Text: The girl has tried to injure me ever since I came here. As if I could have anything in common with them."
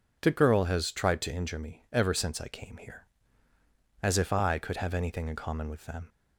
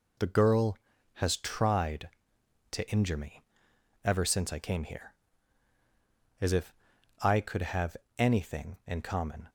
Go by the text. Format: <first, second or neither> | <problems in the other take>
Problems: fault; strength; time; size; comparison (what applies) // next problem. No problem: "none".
first | pauses between "me" and "ever"; noticeable; at 3.4 s; 0.60 s long // pauses between "if" and "I"; noticeable; at 6.7 s; 0.48 s long // pauses between "have" and "anything"; slight; at 7.9 s; 0.22 s long // stops before "with them"; at 9.4 s